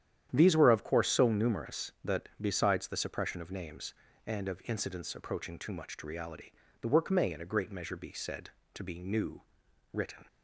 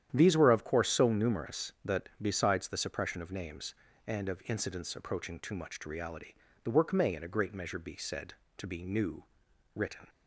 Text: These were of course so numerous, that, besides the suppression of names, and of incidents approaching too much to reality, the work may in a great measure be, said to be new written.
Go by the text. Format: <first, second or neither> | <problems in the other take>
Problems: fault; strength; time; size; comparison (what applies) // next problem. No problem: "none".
neither | starts louder than the rest; strong; the same in both // pauses between "new" and "written"; noticeable; the same in both